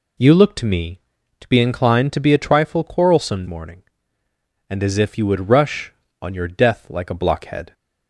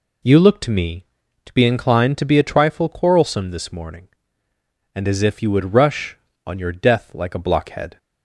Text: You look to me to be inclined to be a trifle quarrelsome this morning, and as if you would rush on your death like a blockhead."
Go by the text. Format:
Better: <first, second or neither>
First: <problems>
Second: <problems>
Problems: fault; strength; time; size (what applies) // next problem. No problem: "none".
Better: second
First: skips "this"; at 3.4 s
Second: none